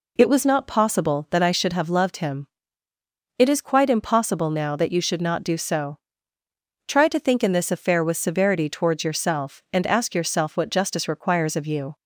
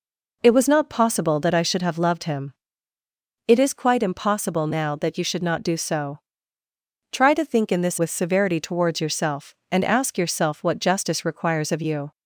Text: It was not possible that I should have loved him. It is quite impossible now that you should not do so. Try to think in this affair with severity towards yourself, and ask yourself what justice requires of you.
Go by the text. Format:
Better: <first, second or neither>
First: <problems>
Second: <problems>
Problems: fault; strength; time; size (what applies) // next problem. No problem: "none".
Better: first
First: none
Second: skips "affair"; at 7.9 s